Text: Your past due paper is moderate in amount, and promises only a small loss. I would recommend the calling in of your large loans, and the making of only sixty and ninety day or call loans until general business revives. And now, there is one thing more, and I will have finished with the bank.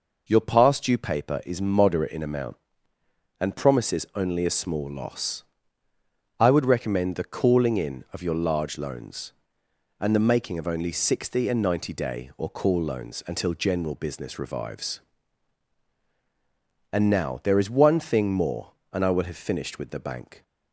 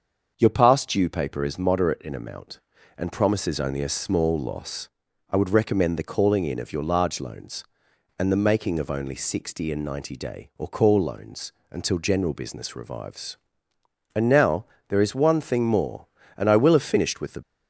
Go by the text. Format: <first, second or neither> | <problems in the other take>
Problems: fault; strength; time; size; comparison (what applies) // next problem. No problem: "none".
first | starts louder than the rest; until 1.3 s; 6.5 dB // pauses between "loans" and "until"; slight; at 11.5 s; 0.18 s long // stops before "bank"; at 17.4 s